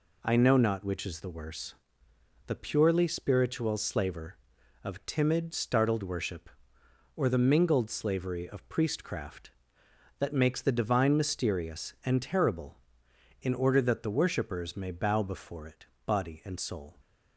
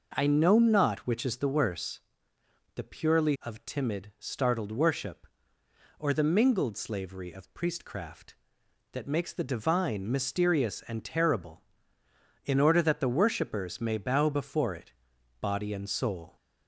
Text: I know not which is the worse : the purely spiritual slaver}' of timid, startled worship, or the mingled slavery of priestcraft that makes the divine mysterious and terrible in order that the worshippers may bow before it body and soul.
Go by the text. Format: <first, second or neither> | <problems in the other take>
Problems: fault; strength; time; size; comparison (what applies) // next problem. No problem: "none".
first | skips "spiritual slaver"; at 3.3 s // pauses between "it" and "body"; noticeable; at 14.9 s; 0.48 s long; slight in the first